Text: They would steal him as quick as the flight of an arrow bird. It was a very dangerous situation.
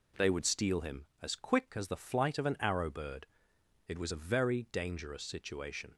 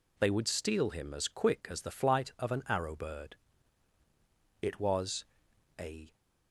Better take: first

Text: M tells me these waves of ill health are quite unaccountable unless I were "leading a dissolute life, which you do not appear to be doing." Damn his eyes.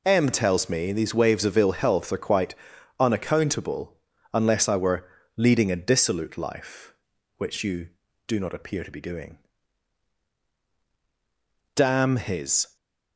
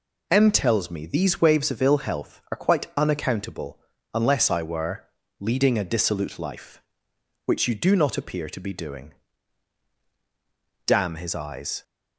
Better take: second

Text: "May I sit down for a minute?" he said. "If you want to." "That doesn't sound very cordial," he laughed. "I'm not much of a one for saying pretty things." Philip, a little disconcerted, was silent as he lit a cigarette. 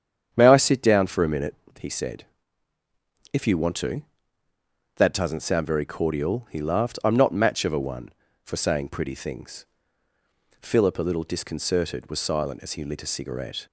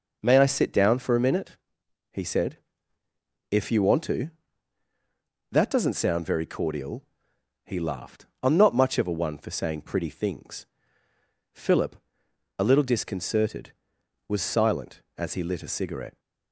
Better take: second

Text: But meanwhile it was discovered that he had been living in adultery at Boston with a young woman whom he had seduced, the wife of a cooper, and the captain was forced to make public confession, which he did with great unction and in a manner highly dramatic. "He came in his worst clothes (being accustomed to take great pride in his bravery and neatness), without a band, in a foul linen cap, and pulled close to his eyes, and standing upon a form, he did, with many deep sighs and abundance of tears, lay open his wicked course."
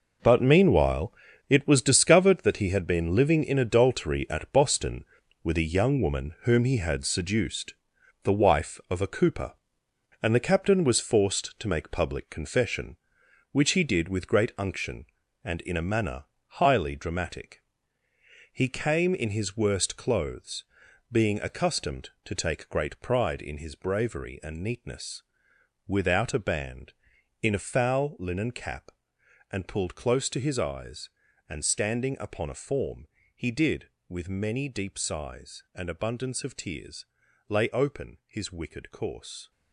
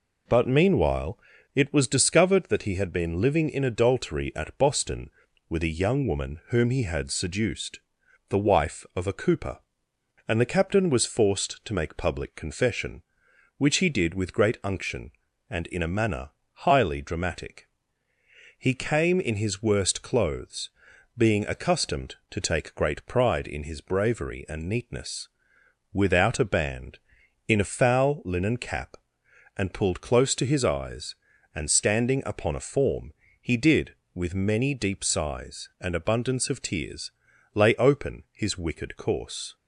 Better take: second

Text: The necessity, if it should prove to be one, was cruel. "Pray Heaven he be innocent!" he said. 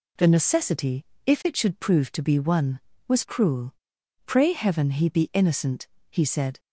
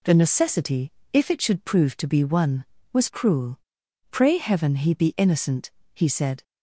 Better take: neither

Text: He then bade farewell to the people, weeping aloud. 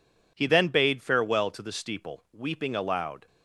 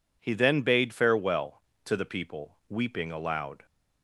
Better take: second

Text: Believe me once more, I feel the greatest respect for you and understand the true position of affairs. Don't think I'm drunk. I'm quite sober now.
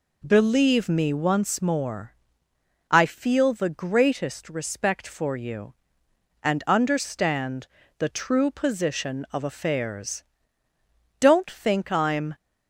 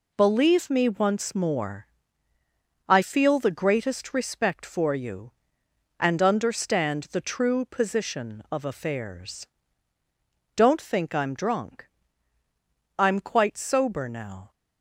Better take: second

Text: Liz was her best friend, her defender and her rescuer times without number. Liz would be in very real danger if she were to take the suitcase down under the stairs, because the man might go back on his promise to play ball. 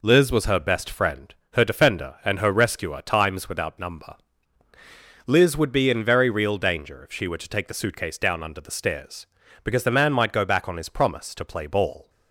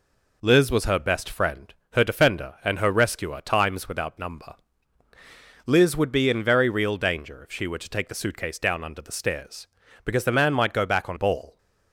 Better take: first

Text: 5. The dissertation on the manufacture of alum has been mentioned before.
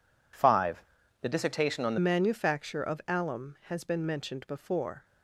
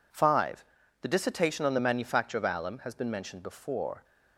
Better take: second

